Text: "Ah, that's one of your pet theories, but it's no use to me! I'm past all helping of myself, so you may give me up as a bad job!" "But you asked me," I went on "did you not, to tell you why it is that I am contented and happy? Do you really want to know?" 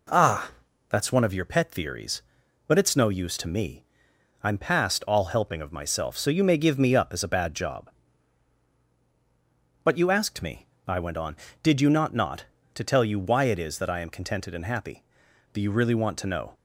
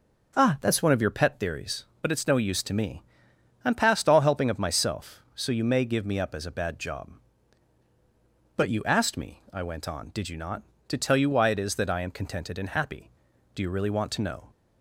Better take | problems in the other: second | says "not" twice; at 12.1 s

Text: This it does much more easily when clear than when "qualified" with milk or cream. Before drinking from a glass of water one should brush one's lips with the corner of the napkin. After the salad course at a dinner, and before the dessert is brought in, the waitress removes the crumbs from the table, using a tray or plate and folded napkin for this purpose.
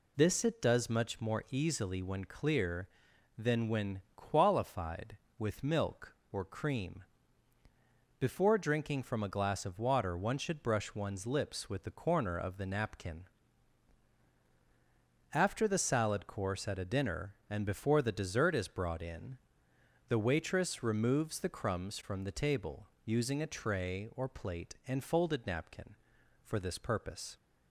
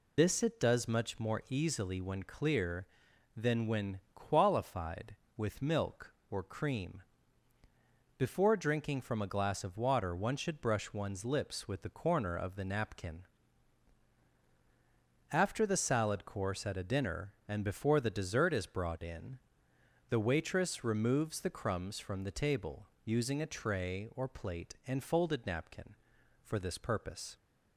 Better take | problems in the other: first | loses the start of "This"; at 0.1 s; 25 ms

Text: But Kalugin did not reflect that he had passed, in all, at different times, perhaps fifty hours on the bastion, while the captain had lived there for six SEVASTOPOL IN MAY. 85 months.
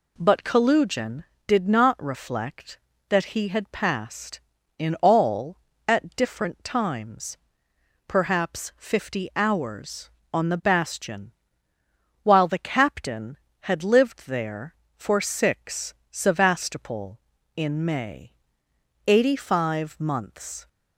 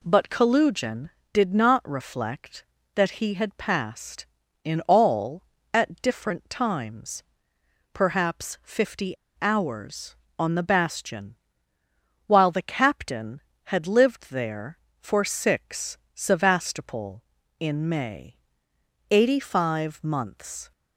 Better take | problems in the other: first | pauses between "fifty" and "hours"; slight; at 9.1 s; 0.25 s long // pauses between "six" and "SEVASTOPOL"; slight; at 15.9 s; 0.16 s long; slight in the first

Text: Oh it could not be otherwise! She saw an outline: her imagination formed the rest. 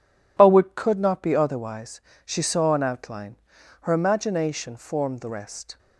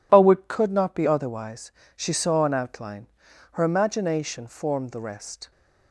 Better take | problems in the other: neither | none

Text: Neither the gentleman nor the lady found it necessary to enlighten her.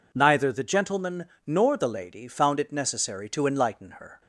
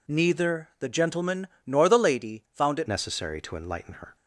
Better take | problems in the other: first | pauses between "gentleman" and "nor"; slight; at 1.4 s; 0.18 s long; slight in the first // changes voice at "necessary"; from 2.8 s on; 1.3 s long

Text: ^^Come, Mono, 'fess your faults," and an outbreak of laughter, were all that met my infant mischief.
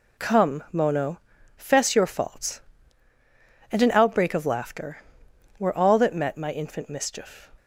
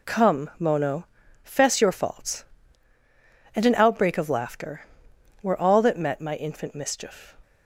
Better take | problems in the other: neither | none

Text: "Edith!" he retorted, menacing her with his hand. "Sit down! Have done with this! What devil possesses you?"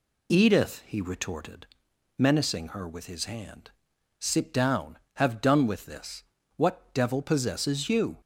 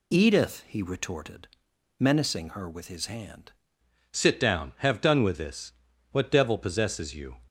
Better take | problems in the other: first | changes voice at "Sit"; from 4.1 s on; 3.2 s long

